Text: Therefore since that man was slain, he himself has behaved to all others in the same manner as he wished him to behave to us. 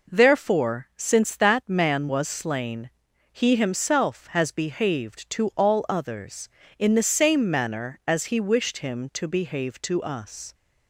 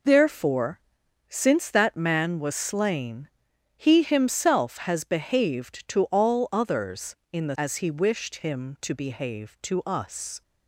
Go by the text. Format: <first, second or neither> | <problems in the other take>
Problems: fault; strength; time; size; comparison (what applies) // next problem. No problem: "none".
first | pauses between "Therefore" and "since"; noticeable; at 0.8 s; 0.52 s long // skips "same manner"; at 7.5 s